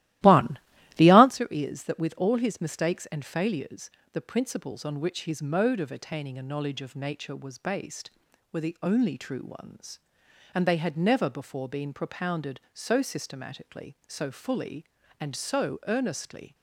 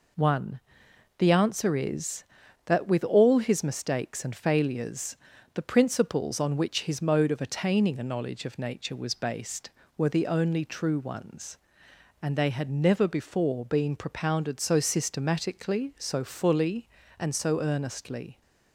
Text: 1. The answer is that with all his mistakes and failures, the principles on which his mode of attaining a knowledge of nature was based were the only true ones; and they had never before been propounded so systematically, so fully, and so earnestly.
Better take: second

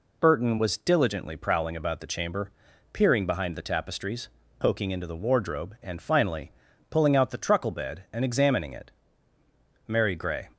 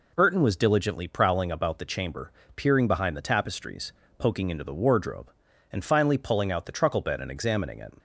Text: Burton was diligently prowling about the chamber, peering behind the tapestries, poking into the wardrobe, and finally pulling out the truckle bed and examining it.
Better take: second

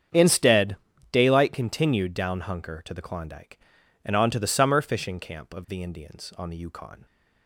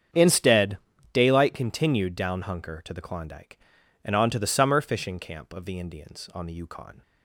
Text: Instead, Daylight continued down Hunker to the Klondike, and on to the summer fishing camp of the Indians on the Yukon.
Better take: neither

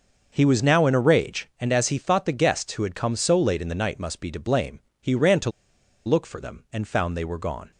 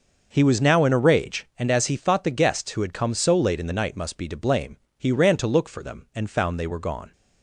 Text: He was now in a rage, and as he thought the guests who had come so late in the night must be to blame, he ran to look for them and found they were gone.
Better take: second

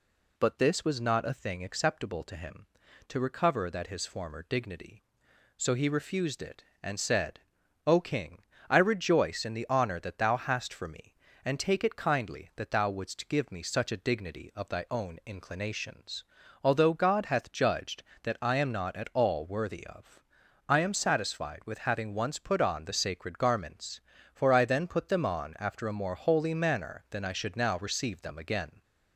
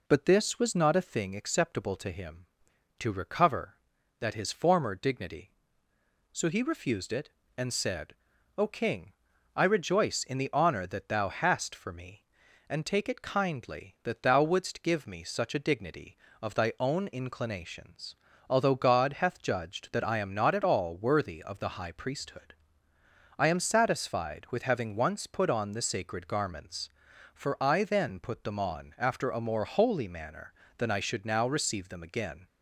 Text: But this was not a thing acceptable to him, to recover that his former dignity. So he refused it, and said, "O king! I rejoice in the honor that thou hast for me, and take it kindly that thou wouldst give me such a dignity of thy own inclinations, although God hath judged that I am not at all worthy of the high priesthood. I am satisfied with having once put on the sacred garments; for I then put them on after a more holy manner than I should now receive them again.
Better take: second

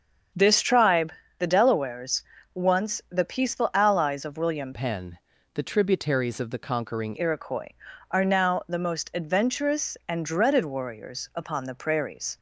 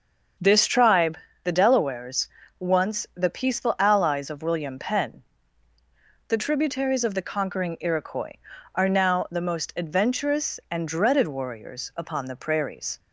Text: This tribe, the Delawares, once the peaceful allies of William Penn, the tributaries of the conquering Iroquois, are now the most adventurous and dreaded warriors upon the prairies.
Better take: second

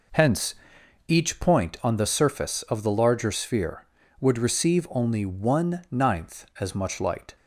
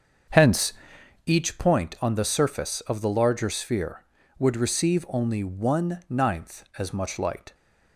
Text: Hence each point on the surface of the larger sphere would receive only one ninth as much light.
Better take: first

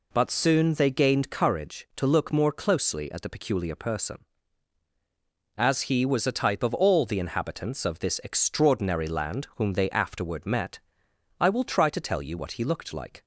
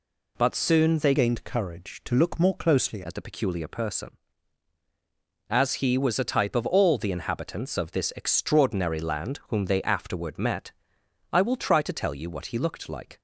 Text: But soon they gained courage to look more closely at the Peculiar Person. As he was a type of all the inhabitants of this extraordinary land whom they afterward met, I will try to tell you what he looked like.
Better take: first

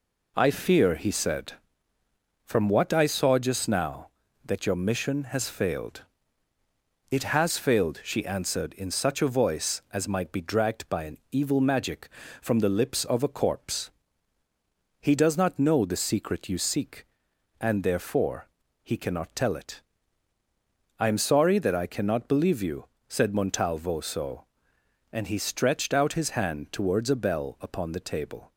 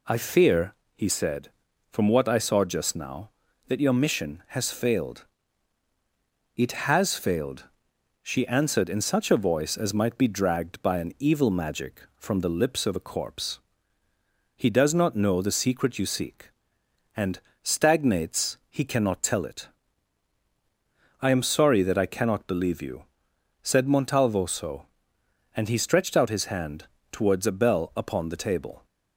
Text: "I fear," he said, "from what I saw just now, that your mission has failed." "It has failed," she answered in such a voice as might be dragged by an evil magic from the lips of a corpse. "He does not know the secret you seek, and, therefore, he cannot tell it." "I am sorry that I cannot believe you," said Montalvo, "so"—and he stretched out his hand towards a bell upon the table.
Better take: first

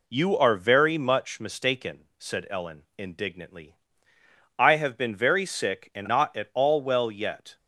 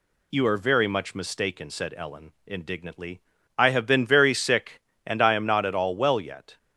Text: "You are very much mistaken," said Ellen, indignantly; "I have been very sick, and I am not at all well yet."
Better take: second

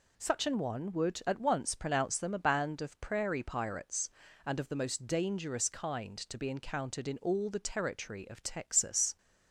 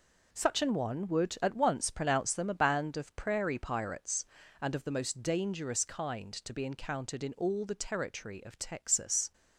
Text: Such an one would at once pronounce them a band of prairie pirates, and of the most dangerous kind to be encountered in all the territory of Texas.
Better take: first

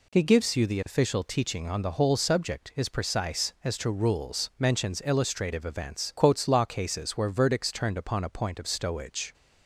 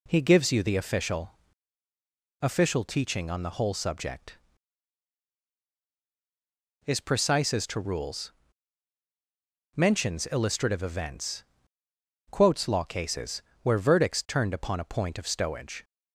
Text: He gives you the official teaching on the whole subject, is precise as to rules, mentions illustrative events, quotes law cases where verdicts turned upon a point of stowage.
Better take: first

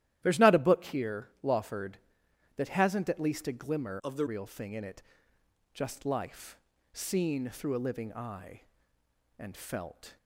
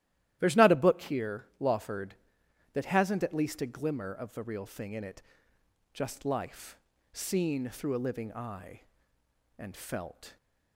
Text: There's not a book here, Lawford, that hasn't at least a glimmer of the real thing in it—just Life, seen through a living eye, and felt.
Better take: second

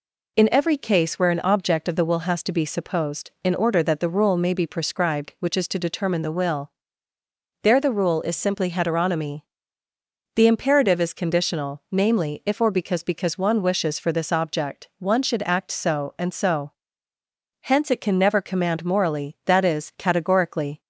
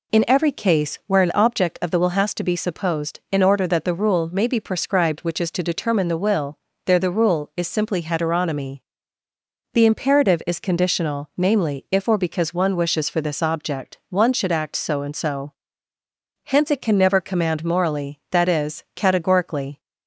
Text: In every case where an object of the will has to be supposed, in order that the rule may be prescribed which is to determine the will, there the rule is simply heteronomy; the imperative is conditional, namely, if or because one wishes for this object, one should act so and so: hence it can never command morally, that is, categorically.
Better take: second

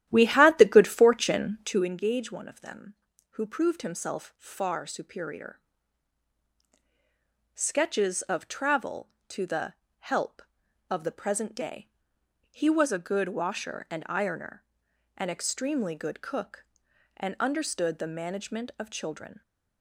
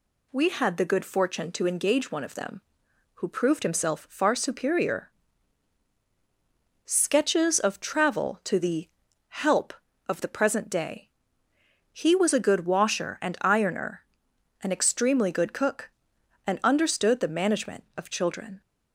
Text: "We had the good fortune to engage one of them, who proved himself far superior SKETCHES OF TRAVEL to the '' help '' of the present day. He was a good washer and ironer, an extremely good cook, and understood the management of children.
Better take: second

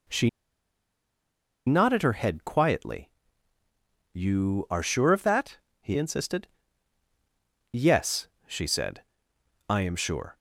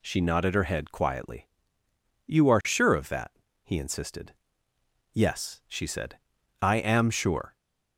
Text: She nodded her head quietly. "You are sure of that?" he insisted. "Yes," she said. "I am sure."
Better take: second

